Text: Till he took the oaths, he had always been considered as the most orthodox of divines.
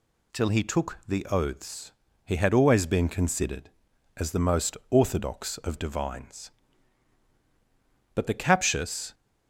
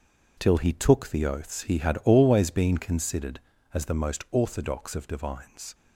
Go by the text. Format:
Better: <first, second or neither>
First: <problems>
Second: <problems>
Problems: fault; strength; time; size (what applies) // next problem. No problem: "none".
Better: second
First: goes on to say "But the captious"; noticeable; from 8.1 s on; 1.0 s long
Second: none